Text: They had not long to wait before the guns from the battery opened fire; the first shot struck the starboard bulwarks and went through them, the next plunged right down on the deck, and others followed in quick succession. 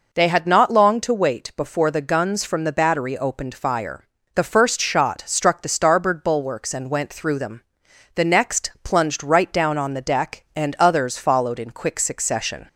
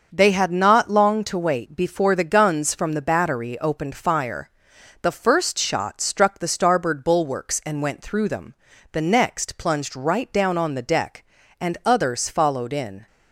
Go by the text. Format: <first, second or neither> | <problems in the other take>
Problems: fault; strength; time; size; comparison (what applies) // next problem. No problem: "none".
first | starts louder than the rest; until 1.1 s; 6.5 dB // stops before "quick succession"; at 13.0 s